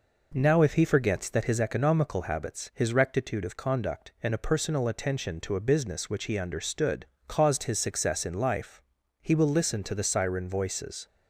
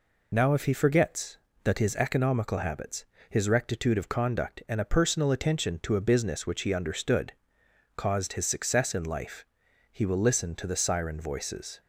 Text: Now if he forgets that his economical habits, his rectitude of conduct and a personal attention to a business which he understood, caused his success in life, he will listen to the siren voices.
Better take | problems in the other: first | loses the start of "Now"; at 0.3 s; 50 ms

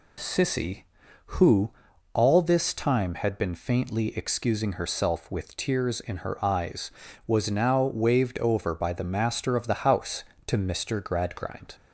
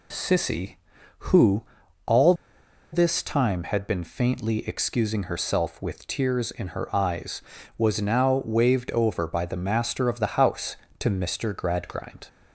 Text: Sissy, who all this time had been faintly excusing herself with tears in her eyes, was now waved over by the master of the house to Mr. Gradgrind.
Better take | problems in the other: first | pauses between "who" and "all"; at 1.6 s; 0.42 s long; also in the first // pauses between "all" and "this"; noticeable; at 2.3 s; 0.59 s long

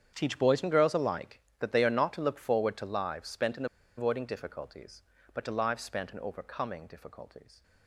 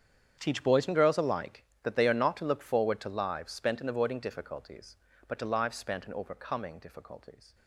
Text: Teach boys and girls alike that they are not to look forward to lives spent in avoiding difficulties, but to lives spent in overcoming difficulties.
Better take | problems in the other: second | starts louder than the rest; strong; until 1.1 s; 8.5 dB; strong in the second // pauses between "in" and "avoiding"; slight; at 3.6 s; 0.32 s long

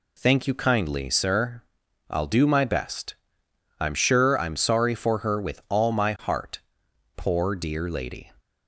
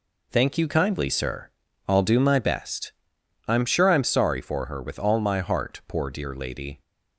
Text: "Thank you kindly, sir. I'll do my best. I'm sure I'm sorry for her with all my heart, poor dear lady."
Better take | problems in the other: neither | none

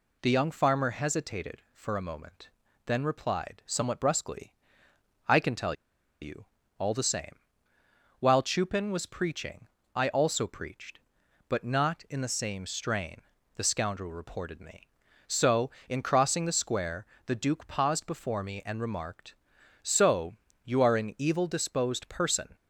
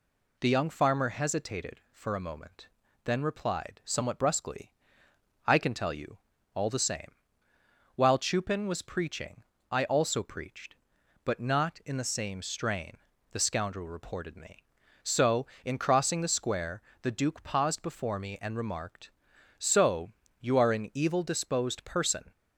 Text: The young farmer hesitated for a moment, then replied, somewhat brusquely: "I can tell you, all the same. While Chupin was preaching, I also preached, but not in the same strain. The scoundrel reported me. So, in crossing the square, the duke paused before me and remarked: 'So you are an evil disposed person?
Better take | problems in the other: second | pauses between "tell" and "you"; noticeable; at 5.7 s; 0.48 s long // pauses between "So" and "you"; slight; at 20.3 s; 0.28 s long; slight in the second

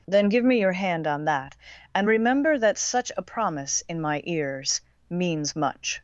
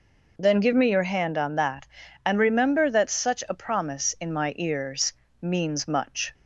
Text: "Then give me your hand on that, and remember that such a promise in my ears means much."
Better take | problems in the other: neither | pauses between "ears" and "means"; slight; the same in both

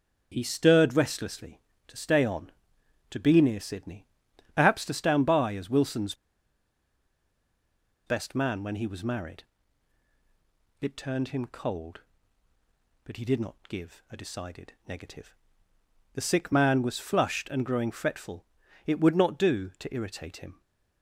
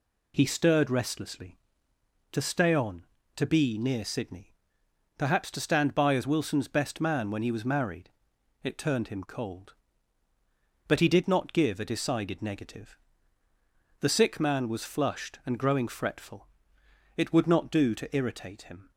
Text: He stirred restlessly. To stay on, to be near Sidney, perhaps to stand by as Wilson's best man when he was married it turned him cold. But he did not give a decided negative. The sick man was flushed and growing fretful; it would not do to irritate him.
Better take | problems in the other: second | starts louder than the rest; until 1.3 s; 7 dB // pauses between "Wilson's" and "best"; strong; at 6.1 s; 1.9 s long // pauses between "married" and "it"; strong; at 9.4 s; 1.3 s long; noticeable in the second // pauses between "decided" and "negative"; slight; at 14.7 s; 0.16 s long

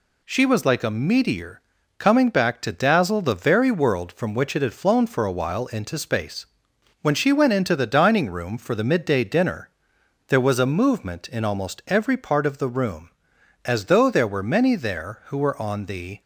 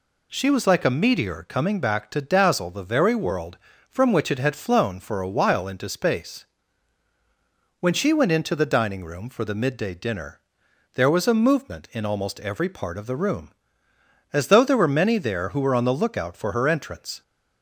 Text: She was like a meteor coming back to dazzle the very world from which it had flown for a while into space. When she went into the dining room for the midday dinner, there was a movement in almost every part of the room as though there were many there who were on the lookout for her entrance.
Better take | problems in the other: second | pauses between "meteor" and "coming"; at 1.5 s; 0.38 s long // stops before "lookout for her entrance"; at 16.2 s

